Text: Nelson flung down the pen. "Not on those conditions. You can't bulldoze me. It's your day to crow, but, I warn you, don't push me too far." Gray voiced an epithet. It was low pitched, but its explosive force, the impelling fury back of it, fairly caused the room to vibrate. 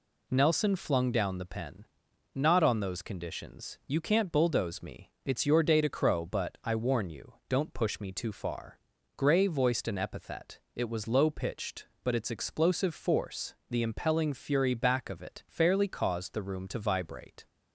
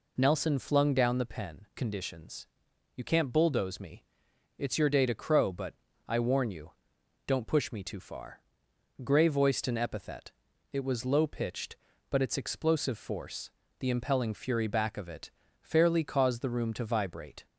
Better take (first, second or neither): first